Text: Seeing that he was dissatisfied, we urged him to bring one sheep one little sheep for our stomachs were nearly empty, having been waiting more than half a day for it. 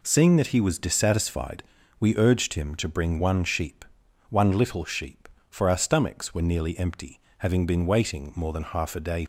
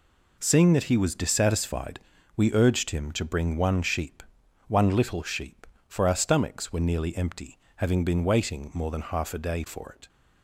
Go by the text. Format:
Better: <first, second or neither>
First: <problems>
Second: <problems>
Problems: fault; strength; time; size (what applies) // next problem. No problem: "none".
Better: second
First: pauses between "sheep" and "one"; noticeable; at 3.8 s; 0.46 s long // stops before "for it"; at 9.2 s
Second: pauses between "sheep" and "one"; noticeable; at 4.2 s; 0.46 s long